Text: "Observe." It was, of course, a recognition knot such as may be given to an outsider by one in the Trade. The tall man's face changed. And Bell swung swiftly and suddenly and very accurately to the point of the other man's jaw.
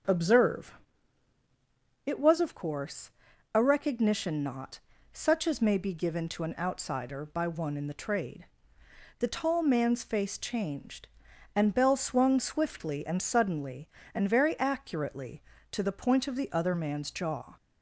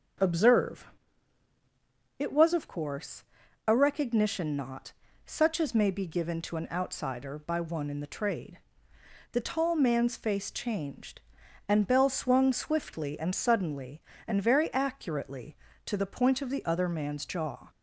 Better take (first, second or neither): neither